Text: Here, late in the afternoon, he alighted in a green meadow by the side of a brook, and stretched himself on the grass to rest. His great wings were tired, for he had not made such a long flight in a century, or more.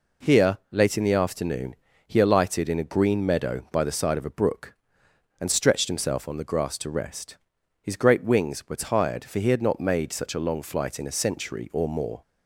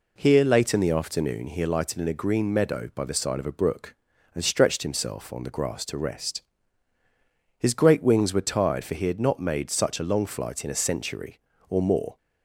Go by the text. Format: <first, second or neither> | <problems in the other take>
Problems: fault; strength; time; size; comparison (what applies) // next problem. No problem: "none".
neither | none